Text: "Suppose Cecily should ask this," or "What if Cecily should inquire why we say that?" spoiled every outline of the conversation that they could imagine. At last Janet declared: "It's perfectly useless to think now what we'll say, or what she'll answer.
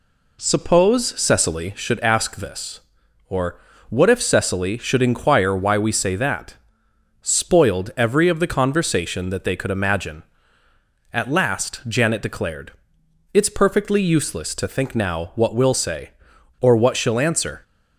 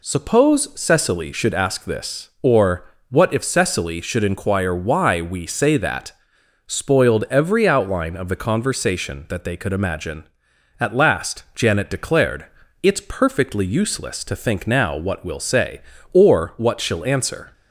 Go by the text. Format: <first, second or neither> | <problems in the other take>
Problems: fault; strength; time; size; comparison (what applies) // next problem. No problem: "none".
second | pauses between "or" and "What"; slight; at 3.5 s; 0.30 s long; slight in the second // skips "outline"; at 8.2 s